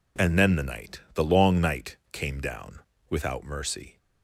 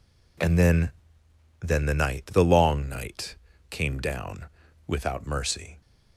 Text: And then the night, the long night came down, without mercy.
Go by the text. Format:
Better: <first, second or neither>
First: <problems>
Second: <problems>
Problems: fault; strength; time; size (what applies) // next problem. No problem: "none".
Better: first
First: none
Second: says "then" twice; at 1.6 s // pauses between "night" and "came"; slight; at 3.3 s; 0.36 s long